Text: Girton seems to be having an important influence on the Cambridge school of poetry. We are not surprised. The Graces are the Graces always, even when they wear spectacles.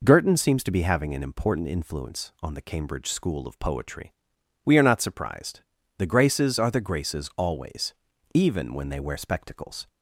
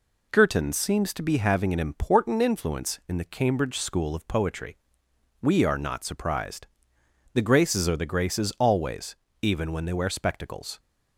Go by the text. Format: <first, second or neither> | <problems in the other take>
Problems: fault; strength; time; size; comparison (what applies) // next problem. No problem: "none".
first | says "in" for "on"; at 3.0 s